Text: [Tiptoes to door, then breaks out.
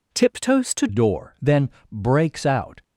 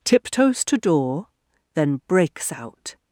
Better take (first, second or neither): second